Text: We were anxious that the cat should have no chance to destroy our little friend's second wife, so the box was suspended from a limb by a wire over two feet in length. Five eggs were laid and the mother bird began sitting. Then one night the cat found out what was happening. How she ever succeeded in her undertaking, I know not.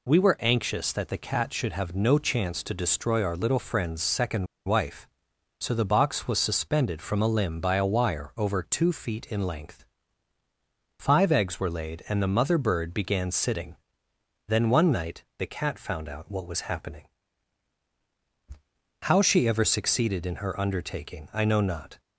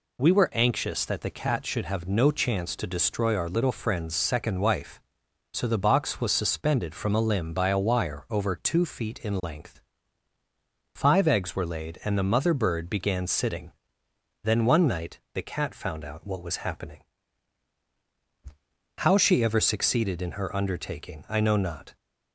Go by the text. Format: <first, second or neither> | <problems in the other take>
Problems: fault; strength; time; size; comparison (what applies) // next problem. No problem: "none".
second | pauses between "second" and "wife"; slight; at 4.4 s; 0.21 s long